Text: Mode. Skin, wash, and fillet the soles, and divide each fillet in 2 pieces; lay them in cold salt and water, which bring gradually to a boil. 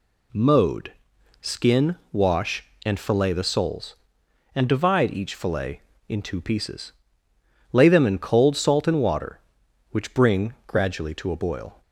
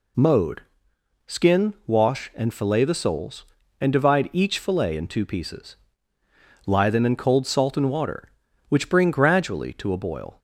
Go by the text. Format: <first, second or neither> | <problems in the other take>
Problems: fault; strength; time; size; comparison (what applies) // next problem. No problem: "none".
first | says "lie" for "lay"; at 6.6 s